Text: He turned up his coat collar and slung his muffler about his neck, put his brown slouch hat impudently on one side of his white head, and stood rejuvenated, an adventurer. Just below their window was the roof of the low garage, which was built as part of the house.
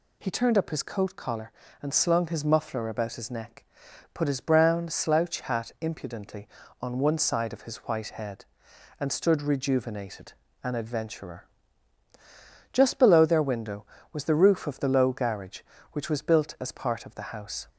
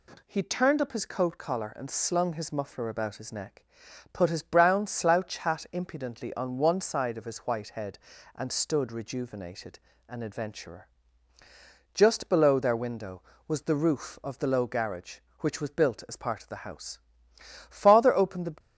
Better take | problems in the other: first | goes on to say "Father opened the"; noticeable; from 17.6 s on; 0.86 s long

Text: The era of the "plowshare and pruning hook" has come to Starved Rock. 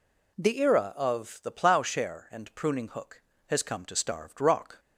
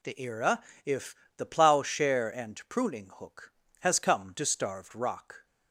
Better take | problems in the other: first | says "if" for "of"; at 0.8 s

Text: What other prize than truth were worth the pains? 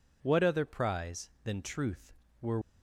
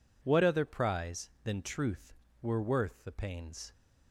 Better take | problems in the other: second | stops before "worth the pains"; at 2.6 s

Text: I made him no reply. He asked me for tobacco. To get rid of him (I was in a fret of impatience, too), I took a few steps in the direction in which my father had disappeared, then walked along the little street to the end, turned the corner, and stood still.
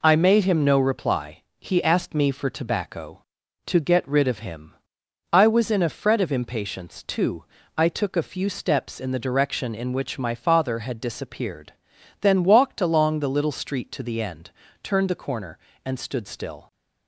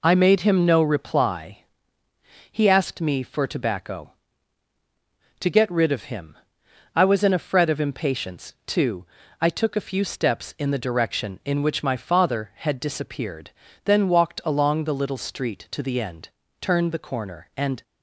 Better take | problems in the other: first | stops before "stood still"; at 17.8 s

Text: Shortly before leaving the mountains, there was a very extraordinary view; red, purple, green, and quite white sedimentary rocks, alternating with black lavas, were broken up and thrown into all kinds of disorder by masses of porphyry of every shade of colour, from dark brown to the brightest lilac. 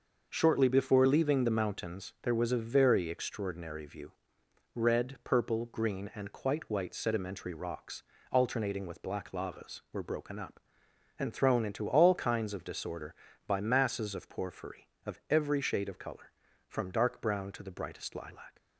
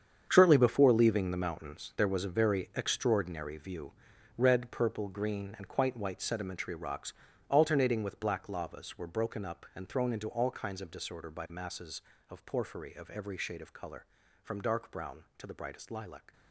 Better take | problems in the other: first | gets quieter; strong; throughout; 12 dB

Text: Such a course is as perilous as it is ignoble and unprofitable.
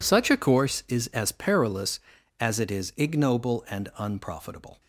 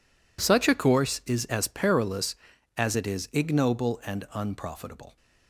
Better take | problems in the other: neither | none

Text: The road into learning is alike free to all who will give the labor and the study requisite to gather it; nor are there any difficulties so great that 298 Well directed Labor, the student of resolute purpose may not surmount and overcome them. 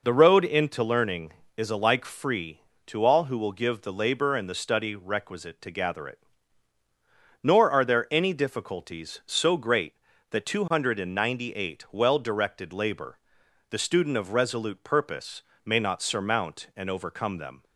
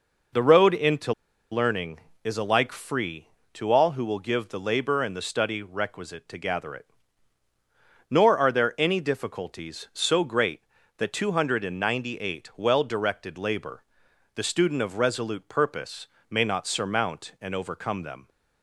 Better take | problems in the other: first | pauses between "into" and "learning"; at 1.1 s; 0.38 s long // pauses between "purpose" and "may"; slight; at 16.0 s; 0.24 s long; slight in the first

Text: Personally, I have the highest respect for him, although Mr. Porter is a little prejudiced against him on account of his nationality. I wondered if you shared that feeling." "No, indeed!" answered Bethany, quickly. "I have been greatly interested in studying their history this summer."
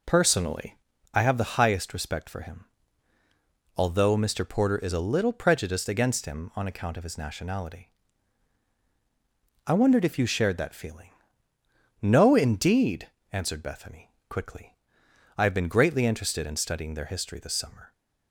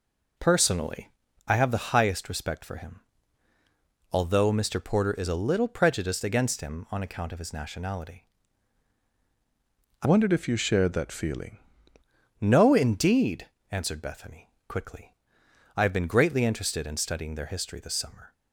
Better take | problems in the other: first | changes voice from "wondered" to "feeling"; from 10.0 to 11.5 s; 1.5 s long

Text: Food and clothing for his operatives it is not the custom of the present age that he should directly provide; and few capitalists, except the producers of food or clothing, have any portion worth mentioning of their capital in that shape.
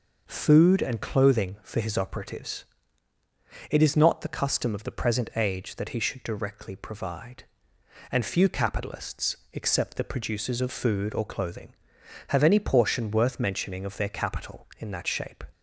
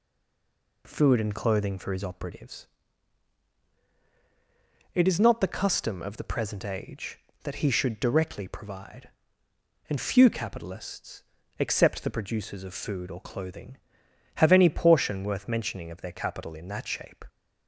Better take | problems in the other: first | stays silent before the first word; slight; until 0.8 s; 0.8 s long // pauses between "operatives" and "it"; strong; at 2.6 s; 2.2 s long; also in the first

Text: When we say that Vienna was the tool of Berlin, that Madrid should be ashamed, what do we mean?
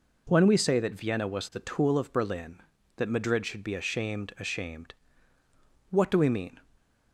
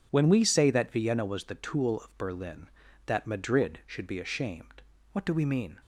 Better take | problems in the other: second | says "ashamed" twice; at 4.3 s

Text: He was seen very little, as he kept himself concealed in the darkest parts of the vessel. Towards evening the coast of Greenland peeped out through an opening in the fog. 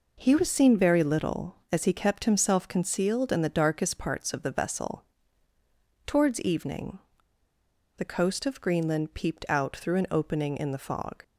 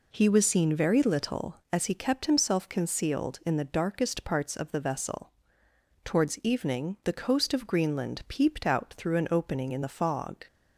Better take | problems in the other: second | pauses between "evening" and "the"; noticeable; at 6.9 s; 0.97 s long

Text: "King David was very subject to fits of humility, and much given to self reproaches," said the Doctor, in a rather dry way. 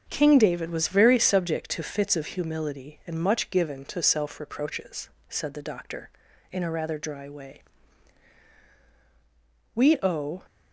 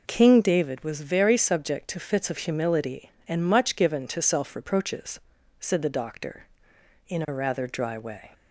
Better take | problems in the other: second | starts louder than the rest; until 1.1 s; 7 dB // goes on to say "We owe"; noticeable; from 9.7 s on; 0.70 s long

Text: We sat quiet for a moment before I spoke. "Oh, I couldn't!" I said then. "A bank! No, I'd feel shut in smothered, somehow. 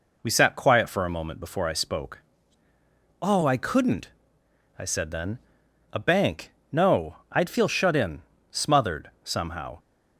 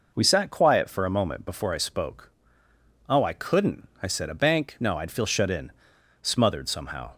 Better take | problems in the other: first | skips "then"; at 4.2 s // pauses between "in" and "smothered"; noticeable; at 5.7 s; 0.48 s long; slight in the first

